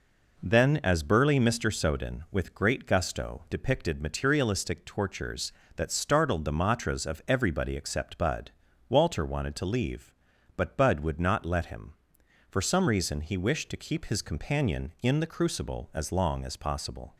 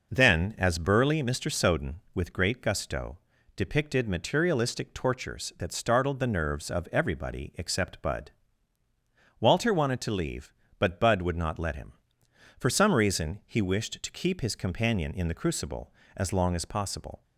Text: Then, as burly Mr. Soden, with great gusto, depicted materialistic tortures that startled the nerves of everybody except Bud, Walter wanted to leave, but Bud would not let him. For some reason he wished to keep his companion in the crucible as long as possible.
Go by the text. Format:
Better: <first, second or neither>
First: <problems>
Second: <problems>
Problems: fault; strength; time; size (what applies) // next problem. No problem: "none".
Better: second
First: says "matras" for "nerves"; at 6.5 s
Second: none